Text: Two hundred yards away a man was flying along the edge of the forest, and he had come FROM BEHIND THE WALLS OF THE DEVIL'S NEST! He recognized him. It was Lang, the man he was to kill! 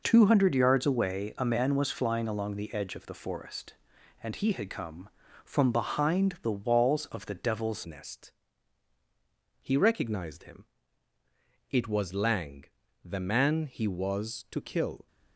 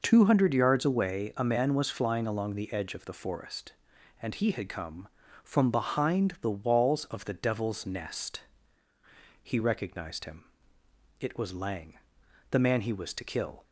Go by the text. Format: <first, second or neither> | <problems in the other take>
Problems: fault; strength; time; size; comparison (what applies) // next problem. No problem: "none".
second | changes voice at "NEST"; from 7.8 s on; 7.2 s long